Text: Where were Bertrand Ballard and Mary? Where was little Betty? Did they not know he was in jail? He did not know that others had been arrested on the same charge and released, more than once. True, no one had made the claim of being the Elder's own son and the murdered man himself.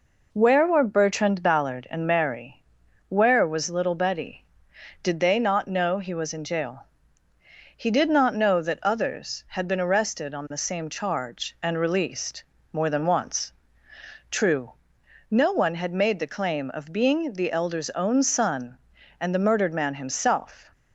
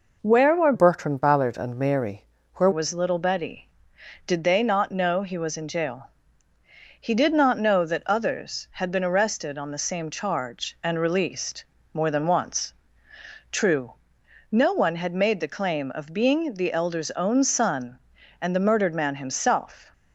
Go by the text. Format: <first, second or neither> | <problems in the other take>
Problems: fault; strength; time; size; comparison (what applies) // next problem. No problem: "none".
first | changes voice from "Bertrand" to "Where"; from 0.7 to 2.6 s; 1.9 s long